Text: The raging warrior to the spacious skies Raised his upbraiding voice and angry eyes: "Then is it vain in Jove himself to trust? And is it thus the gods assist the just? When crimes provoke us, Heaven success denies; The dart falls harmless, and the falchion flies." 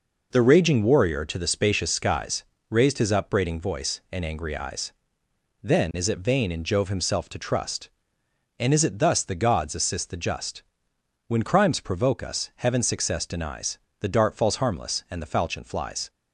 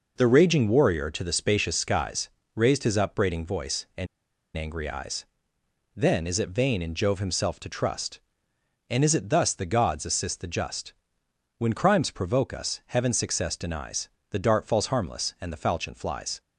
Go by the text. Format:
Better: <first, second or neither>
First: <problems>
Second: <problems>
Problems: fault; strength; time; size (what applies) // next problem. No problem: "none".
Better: first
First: pauses between "skies" and "Raised"; slight; at 2.4 s; 0.26 s long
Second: pauses between "skies" and "Raised"; slight; at 2.2 s; 0.26 s long // pauses between "and" and "angry"; noticeable; at 4.0 s; 0.49 s long